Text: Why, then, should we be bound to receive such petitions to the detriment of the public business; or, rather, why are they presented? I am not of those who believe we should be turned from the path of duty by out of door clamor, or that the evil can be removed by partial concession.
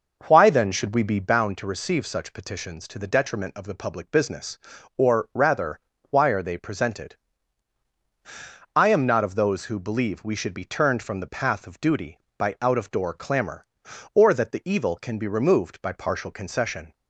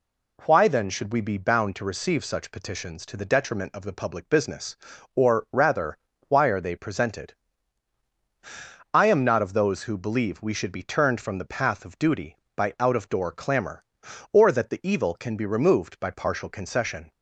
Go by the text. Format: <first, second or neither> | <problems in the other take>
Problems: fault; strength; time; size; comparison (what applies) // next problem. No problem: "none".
second | starts louder than the rest; noticeable; until 1.4 s; 5.5 dB